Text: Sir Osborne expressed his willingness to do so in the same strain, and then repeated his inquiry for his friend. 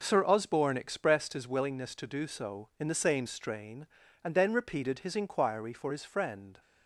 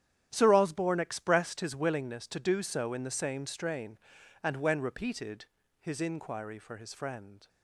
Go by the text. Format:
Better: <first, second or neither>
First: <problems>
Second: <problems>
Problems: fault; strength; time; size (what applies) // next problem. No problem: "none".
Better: first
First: none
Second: starts louder than the rest; strong; until 1.3 s; 10 dB // says "when" for "then"; at 4.5 s // pauses between "repeated" and "his"; slight; at 5.4 s; 0.34 s long